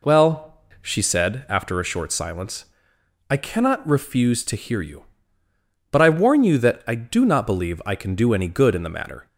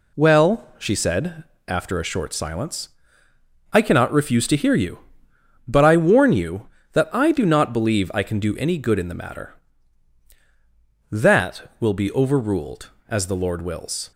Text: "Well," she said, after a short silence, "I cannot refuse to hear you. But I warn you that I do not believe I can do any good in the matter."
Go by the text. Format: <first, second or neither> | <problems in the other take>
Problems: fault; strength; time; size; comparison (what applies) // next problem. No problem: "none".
first | goes on to say "That will be overruled as the Lord wills"; strong; from 11.1 s on; 3.0 s long